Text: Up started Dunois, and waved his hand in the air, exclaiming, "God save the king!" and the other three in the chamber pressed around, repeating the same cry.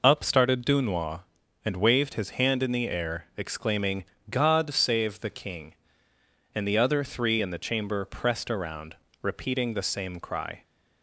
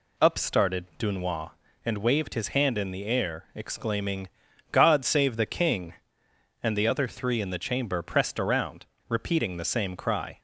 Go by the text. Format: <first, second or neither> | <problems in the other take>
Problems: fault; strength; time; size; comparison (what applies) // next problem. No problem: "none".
neither | none